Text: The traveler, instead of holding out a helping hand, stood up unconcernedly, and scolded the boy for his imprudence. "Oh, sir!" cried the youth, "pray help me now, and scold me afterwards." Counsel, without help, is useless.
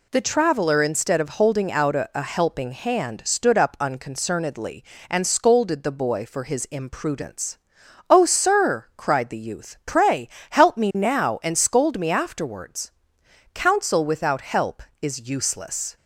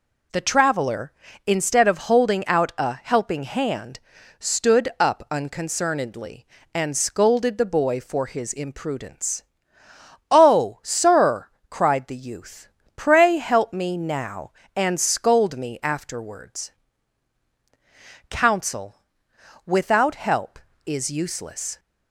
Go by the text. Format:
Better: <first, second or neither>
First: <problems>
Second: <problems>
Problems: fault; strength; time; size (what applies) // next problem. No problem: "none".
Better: second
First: says "a" twice; at 2.1 s // pauses between "pray" and "help"; slight; at 10.2 s; 0.22 s long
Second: none